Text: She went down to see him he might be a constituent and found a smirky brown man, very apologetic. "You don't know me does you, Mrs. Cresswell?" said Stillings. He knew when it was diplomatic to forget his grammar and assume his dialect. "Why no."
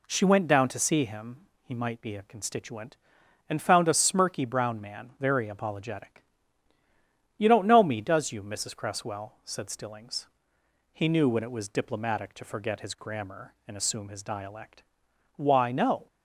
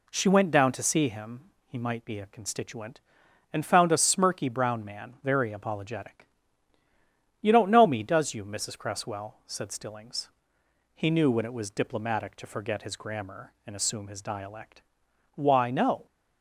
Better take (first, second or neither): neither